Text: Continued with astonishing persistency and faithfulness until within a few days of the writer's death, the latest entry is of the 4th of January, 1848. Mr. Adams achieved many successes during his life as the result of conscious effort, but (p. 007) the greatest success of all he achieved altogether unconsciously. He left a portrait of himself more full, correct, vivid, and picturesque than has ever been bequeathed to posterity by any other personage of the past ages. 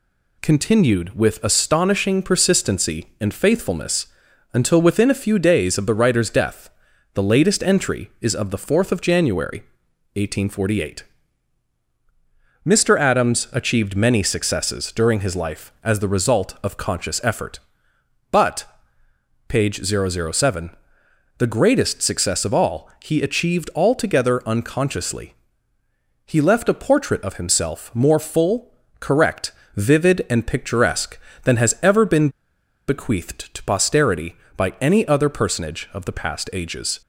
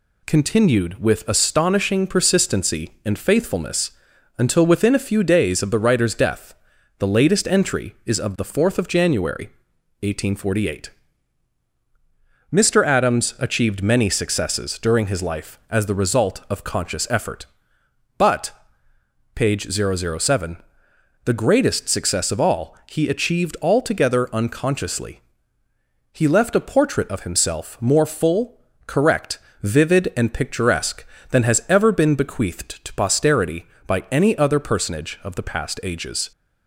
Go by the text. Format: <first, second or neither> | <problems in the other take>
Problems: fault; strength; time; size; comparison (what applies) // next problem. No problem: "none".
second | pauses between "faithfulness" and "until"; noticeable; at 4.0 s; 0.46 s long; noticeable in the second // pauses between "been" and "bequeathed"; noticeable; at 32.2 s; 0.59 s long